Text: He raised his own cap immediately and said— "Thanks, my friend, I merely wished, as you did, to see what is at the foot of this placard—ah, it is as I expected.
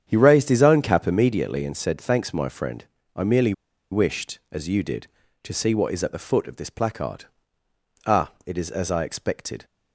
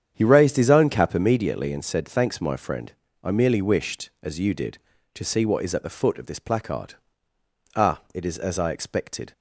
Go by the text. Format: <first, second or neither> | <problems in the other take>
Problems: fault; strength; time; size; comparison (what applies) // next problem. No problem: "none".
second | starts louder than the rest; strong; until 1.0 s; 8.5 dB; strong in the second // pauses between "merely" and "wished"; at 3.5 s; 0.39 s long